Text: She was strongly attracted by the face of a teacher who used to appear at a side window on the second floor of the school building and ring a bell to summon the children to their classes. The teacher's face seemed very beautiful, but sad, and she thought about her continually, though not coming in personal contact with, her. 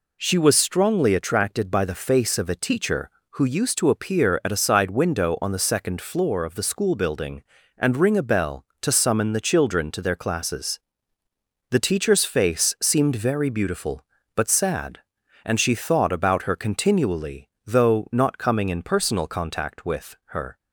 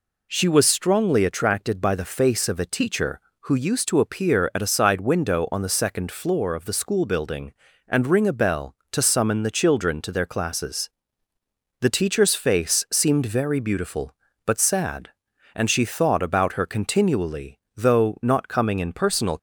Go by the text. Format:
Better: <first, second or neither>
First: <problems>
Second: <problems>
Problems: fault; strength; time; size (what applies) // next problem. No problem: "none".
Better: first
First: none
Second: stops before "contact with her"; at 19.3 s